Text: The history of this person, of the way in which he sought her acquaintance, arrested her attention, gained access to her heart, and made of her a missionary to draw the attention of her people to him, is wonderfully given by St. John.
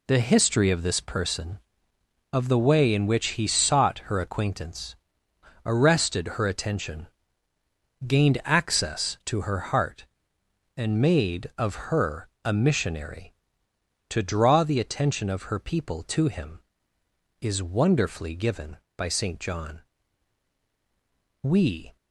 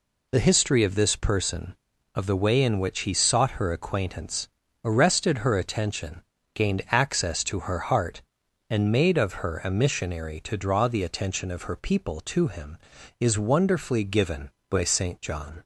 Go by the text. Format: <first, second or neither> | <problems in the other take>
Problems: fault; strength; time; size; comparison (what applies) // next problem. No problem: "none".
second | pauses between "her" and "a"; slight; at 12.2 s; 0.16 s long // goes on to say "We"; from 21.4 s on; 0.54 s long